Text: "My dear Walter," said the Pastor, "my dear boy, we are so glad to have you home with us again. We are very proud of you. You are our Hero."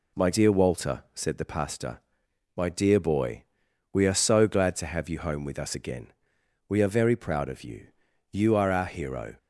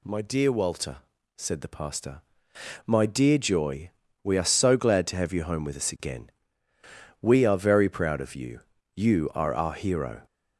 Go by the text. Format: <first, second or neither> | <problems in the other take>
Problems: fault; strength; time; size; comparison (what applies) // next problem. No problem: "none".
first | says "joy" for "boy"; at 3.3 s